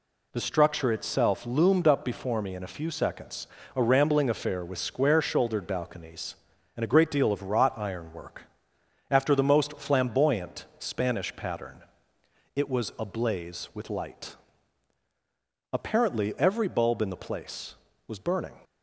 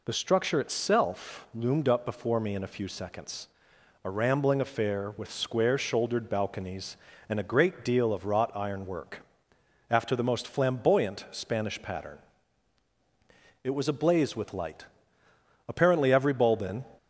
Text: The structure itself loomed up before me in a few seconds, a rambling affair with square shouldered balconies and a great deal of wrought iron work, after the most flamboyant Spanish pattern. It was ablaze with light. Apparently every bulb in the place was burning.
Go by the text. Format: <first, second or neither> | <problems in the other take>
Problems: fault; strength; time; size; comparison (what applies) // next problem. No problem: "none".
first | stops before "the place was burning"; at 16.9 s